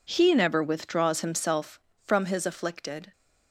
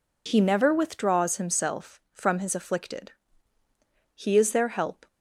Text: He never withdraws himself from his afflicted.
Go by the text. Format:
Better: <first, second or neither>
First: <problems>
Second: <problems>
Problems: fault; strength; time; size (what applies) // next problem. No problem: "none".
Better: first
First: none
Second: goes on to say "He is their help"; noticeable; from 4.1 s on; 0.92 s long